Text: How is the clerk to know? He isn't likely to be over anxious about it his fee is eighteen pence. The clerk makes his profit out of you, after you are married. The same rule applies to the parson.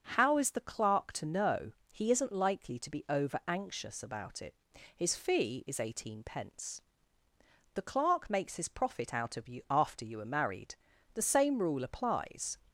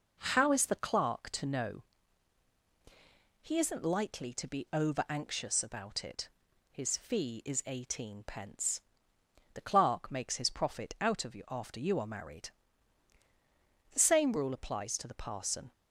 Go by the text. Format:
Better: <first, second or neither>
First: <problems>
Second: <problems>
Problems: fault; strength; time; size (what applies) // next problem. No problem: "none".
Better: second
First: starts louder than the rest; noticeable; until 1.1 s; 6 dB // pauses between "it" and "his"; at 4.5 s; 0.40 s long // stops before "to the parson"; at 12.6 s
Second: pauses between "it" and "his"; at 6.2 s; 0.42 s long